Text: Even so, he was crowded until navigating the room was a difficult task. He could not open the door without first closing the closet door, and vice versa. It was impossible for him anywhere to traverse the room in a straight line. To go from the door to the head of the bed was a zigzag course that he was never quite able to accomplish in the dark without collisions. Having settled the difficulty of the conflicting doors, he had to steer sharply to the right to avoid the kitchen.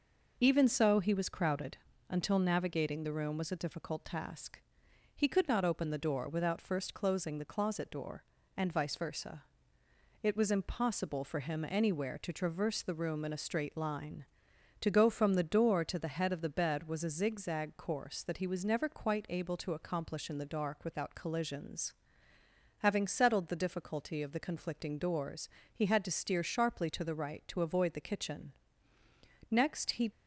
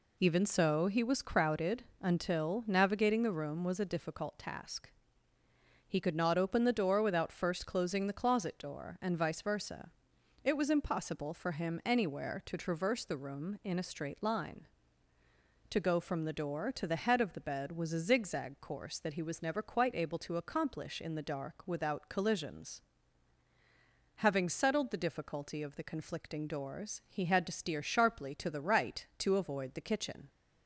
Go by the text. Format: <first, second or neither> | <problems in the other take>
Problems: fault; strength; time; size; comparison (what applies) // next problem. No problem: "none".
second | pauses between "crowded" and "until"; slight; at 1.7 s; 0.32 s long; slight in the second // goes on to say "Next he"; noticeable; from 29.4 s on; 0.62 s long